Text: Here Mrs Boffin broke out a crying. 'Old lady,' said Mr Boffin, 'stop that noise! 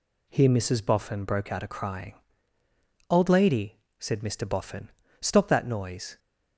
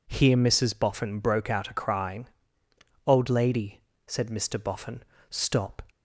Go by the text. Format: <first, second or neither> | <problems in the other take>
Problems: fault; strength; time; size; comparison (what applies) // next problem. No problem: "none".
first | stops before "that noise"; at 5.8 s